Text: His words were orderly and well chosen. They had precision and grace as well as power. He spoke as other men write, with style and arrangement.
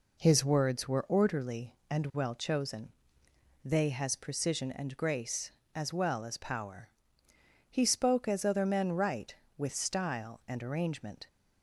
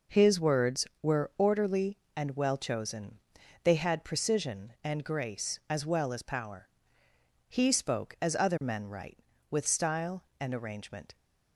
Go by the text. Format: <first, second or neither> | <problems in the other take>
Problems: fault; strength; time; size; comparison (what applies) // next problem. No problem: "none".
second | says "has" for "had"; at 3.8 s